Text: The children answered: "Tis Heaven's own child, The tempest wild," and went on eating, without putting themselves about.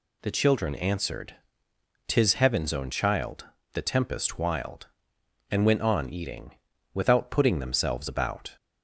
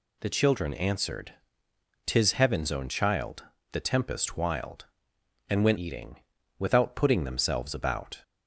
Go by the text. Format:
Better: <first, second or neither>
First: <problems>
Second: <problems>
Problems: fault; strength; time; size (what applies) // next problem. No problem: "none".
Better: first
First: none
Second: skips "on"; at 5.7 s